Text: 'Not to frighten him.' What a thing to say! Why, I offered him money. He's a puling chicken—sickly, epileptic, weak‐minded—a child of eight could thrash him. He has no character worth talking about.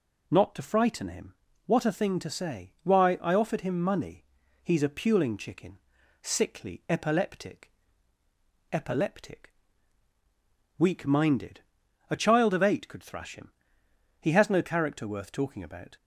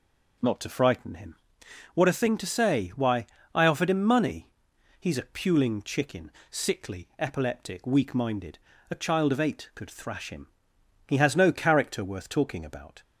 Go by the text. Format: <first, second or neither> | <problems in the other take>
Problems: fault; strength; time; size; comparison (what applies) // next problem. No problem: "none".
second | says "epileptic" twice; at 8.7 s